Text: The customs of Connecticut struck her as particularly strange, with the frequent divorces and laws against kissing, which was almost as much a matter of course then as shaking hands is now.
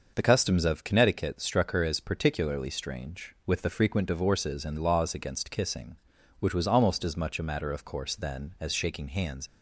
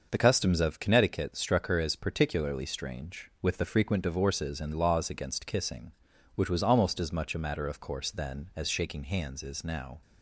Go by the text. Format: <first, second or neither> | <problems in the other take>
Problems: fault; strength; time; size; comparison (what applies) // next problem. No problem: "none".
second | starts louder than the rest; noticeable; until 1.1 s; 6 dB; noticeable in the second // stops before "is now"; at 9.4 s